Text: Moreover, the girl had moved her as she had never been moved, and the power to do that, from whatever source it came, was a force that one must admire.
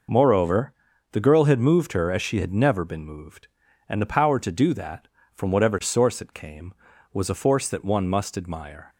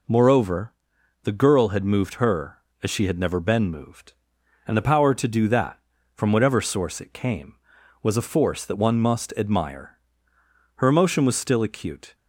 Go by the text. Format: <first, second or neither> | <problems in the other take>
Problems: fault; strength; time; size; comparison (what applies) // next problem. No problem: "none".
first | goes on to say "Her emotion was still acute"; from 10.7 s on; 1.3 s long